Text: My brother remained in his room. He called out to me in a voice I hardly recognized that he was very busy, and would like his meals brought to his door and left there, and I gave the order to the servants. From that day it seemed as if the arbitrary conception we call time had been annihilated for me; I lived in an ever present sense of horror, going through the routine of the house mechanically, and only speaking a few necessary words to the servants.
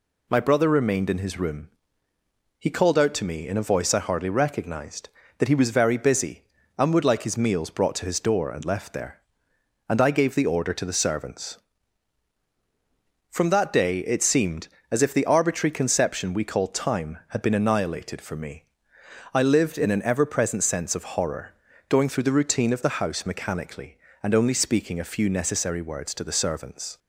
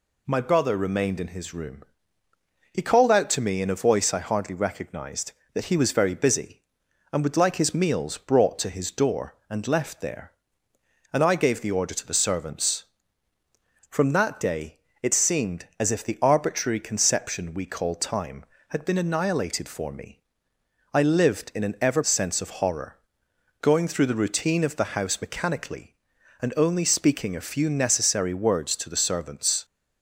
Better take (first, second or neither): first